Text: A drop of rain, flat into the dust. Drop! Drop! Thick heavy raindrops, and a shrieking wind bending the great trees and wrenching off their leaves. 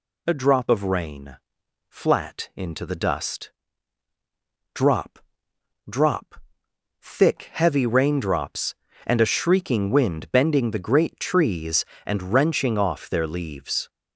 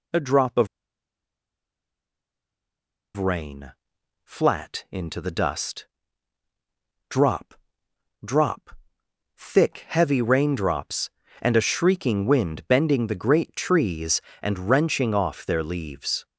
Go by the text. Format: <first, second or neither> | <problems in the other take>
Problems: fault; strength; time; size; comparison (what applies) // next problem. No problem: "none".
first | pauses between "of" and "rain"; strong; at 0.6 s; 2.4 s long